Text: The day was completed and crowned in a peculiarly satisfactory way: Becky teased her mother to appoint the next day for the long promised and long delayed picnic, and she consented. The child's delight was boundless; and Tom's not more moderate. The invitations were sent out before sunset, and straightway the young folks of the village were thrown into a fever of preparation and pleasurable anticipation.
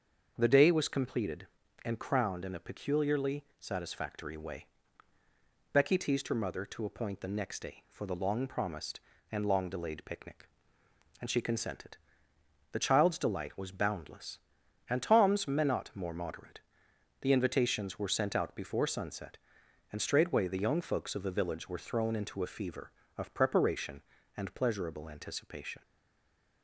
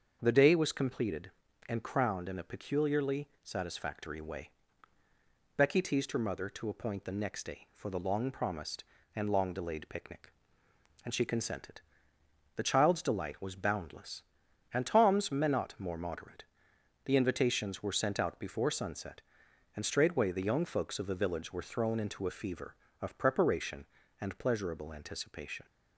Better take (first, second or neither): second